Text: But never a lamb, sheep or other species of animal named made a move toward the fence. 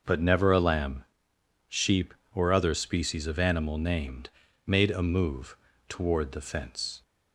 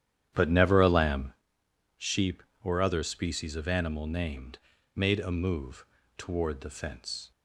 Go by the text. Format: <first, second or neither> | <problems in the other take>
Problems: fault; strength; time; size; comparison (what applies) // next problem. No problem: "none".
first | starts louder than the rest; strong; until 1.4 s; 10 dB // pauses between "named" and "made"; at 4.5 s; 0.38 s long; also in the first // pauses between "move" and "toward"; slight; at 5.8 s; 0.32 s long; slight in the first